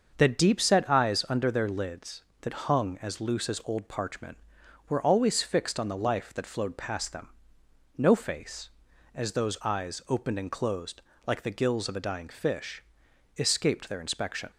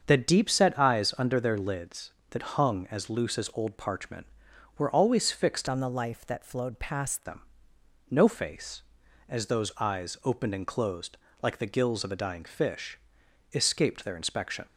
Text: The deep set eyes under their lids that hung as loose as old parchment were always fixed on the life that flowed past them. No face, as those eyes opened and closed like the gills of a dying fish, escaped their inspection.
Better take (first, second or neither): first